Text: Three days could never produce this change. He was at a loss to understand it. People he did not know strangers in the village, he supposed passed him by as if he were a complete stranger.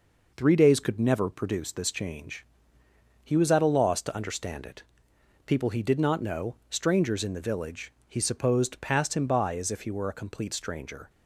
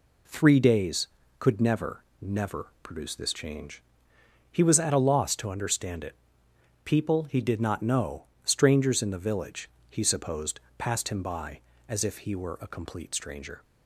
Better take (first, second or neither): first